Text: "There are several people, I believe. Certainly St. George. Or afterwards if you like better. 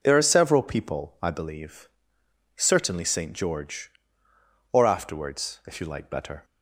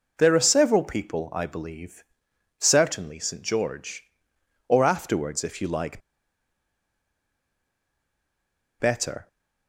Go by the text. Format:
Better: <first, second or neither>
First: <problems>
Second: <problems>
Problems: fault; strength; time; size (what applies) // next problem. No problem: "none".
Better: first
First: none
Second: pauses between "like" and "better"; strong; at 6.0 s; 2.8 s long